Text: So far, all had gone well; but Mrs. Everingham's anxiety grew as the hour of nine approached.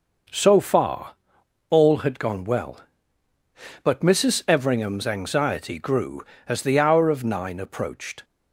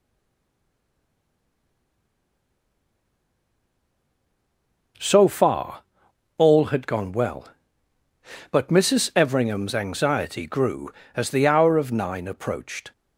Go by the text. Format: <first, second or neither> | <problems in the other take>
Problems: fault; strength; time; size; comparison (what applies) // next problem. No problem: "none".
first | stays silent before the first word; strong; until 4.9 s; 4.9 s long